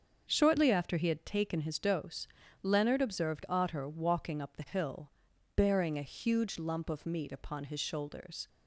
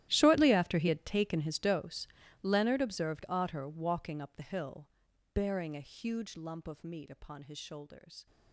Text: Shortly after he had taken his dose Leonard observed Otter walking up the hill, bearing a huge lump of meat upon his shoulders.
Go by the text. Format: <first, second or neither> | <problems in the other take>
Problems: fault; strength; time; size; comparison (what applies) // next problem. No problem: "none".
first | gets quieter; strong; throughout; 19 dB // starts louder than the rest; strong; until 1.1 s; 13.5 dB; also in the first // pauses between "dose" and "Leonard"; slight; at 2.0 s; 0.34 s long; slight in the first